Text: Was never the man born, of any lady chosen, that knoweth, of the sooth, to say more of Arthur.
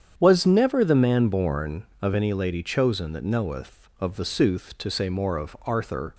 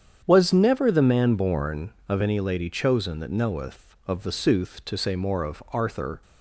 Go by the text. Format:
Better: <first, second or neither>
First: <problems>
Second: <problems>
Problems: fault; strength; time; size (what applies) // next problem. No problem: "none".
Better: neither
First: starts louder than the rest; strong; until 1.1 s; 8.5 dB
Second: starts louder than the rest; strong; until 1.2 s; 8.5 dB